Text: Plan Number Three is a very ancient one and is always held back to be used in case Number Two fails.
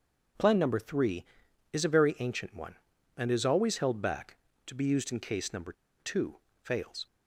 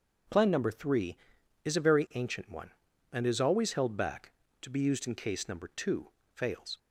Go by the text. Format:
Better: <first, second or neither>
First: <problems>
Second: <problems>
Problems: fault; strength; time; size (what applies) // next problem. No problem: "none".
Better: second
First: pauses between "Number" and "Two"; slight; at 5.7 s; 0.26 s long // pauses between "Two" and "fails"; slight; at 6.3 s; 0.24 s long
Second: pauses between "Two" and "fails"; slight; at 6.0 s; 0.24 s long